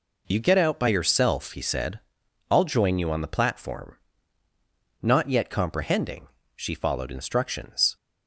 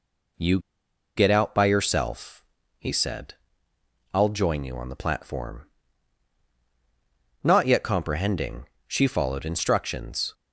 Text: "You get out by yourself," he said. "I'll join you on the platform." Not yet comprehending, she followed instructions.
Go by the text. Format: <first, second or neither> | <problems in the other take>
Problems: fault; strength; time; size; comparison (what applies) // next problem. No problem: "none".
first | pauses between "You" and "get"; noticeable; at 0.5 s; 0.57 s long